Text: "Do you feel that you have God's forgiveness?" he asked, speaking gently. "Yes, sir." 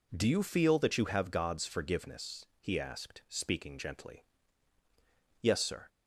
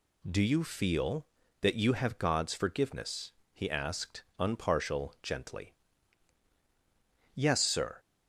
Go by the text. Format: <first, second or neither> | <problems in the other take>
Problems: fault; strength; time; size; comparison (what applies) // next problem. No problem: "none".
first | says "unpartial" for "speaking"; at 4.3 s